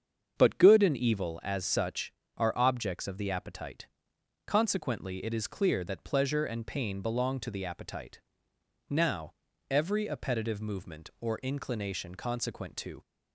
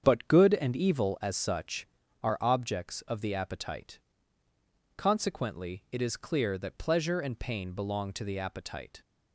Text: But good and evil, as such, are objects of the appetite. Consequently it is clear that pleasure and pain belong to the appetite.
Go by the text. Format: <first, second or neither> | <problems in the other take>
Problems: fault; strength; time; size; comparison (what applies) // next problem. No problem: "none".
second | starts louder than the rest; strong; until 1.3 s; 7.5 dB; strong in the second // goes on to say "Now every appetitive movement or inclination consequent to"; strong; from 8.8 s on; 4.1 s long